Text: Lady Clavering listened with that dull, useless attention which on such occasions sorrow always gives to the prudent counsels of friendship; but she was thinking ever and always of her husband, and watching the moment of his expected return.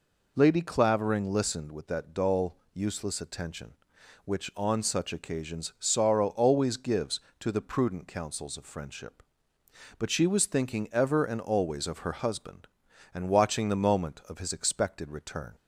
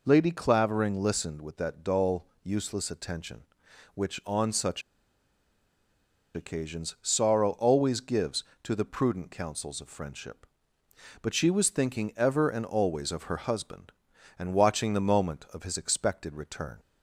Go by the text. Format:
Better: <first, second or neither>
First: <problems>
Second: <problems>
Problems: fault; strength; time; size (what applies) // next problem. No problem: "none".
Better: first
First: none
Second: pauses between "such" and "occasions"; strong; at 4.8 s; 1.5 s long